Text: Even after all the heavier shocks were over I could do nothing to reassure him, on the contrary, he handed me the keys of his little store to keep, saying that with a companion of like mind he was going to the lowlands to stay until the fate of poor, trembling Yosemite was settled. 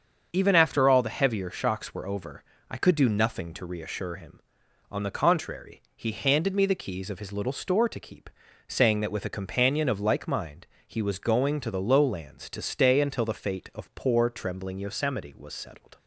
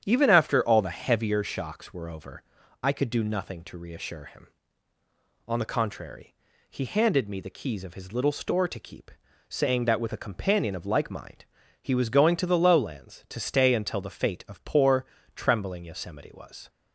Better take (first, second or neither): first